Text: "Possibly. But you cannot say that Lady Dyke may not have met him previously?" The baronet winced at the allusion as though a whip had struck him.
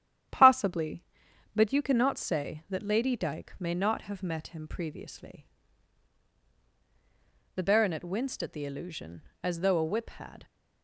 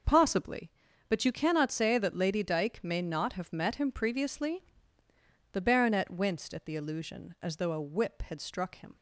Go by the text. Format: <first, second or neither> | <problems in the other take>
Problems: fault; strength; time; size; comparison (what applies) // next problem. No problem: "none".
second | starts louder than the rest; strong; until 1.8 s; 10.5 dB // stops before "struck him"; at 10.4 s